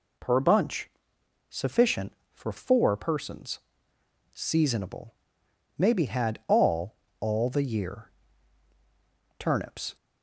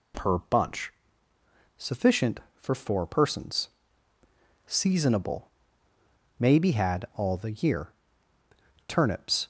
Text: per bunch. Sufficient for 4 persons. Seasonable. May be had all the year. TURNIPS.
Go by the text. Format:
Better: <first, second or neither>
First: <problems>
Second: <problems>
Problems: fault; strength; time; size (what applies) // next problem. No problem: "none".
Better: second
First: says "all" twice; at 7.1 s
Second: none